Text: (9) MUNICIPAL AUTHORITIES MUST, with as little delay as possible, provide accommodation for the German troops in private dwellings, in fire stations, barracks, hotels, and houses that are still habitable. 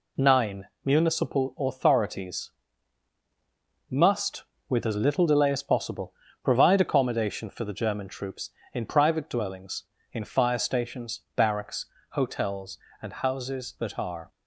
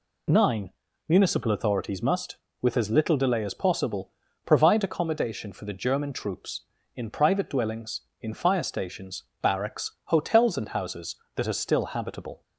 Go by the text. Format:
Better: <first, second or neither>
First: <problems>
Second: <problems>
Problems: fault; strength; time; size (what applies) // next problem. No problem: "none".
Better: second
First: pauses between "AUTHORITIES" and "MUST"; strong; at 2.4 s; 1.4 s long // stops before "still habitable"; at 14.3 s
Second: none